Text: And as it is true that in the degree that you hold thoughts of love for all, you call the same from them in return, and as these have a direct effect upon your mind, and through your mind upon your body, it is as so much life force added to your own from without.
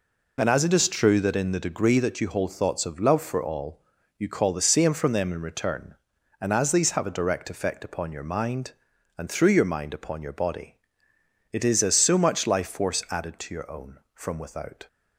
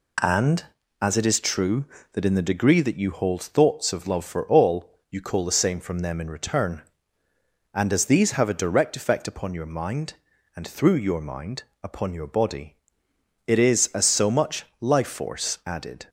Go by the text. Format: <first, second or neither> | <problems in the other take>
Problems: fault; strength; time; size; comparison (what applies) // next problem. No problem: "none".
first | pauses between "mind" and "upon"; slight; at 11.6 s; 0.20 s long // pauses between "much" and "life"; slight; at 14.6 s; 0.16 s long // stops before "to your own from without"; at 16.0 s